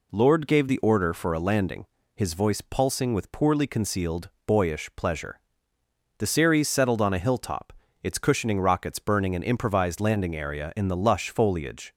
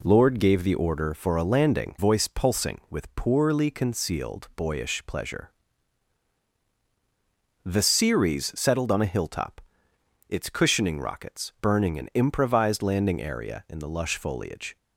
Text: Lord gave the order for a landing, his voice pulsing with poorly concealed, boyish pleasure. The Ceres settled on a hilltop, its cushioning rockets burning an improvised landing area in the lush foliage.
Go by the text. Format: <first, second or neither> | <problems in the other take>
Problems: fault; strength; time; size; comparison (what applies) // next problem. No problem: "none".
first | skips "his"; at 1.9 s